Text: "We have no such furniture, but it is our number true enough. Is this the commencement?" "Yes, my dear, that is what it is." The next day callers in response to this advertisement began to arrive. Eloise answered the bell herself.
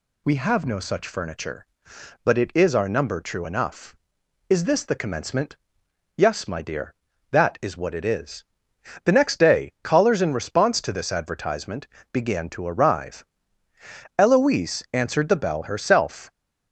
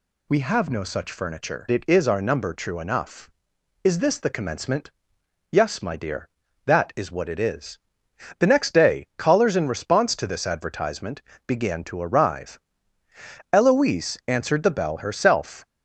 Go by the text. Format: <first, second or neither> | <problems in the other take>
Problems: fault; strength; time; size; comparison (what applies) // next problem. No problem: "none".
first | skips "but"; at 1.7 s // pauses between "advertisement" and "began"; slight; at 11.2 s; 0.24 s long; slight in the first